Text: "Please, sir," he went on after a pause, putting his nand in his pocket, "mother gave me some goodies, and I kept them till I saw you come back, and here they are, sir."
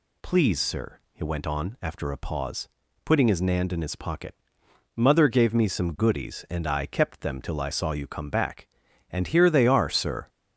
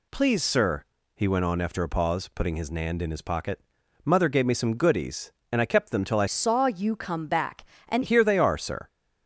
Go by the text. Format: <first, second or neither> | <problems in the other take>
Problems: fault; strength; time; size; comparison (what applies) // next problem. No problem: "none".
first | changes voice from "saw" to "and"; from 6.2 to 8.0 s; 1.8 s long